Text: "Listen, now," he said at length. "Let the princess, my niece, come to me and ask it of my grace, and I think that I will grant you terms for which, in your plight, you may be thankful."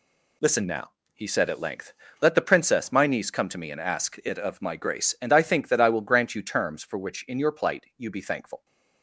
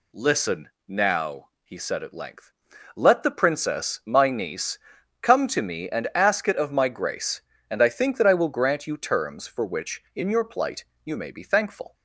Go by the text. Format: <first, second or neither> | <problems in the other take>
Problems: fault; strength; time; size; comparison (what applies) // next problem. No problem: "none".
second | skips "may"; at 8.1 s